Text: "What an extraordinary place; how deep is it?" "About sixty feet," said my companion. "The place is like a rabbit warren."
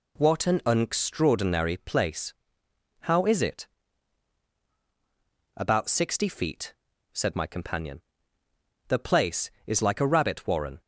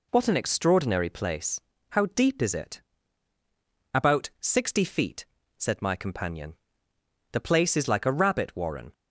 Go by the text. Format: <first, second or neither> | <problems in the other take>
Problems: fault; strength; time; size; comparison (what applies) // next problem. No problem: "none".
second | skips "deep"; at 3.2 s